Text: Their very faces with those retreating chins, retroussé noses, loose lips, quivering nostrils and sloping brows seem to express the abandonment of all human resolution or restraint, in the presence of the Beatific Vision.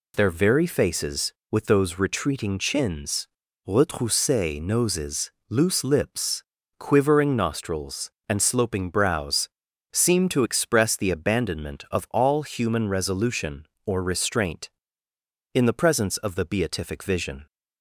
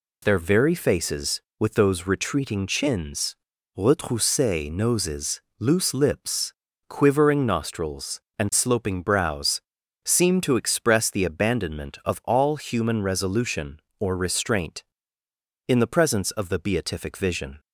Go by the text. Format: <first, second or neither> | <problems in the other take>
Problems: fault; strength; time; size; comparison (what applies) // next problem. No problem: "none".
neither | pauses between "brows" and "seem"; the same in both